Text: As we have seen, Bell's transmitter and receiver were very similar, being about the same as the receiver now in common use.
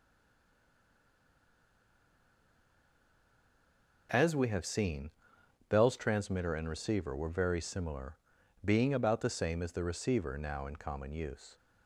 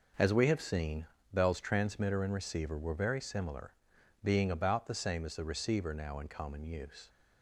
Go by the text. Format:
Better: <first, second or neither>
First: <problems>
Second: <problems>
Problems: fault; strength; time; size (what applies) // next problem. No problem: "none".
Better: second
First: stays silent before the first word; strong; until 4.0 s; 4.0 s long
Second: none